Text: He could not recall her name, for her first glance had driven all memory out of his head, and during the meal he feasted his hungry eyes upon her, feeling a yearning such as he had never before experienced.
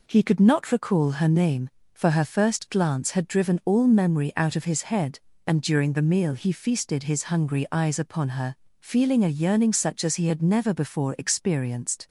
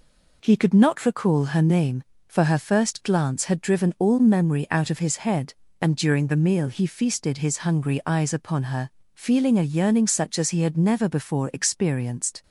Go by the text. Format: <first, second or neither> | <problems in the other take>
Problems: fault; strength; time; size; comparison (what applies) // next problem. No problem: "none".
neither | none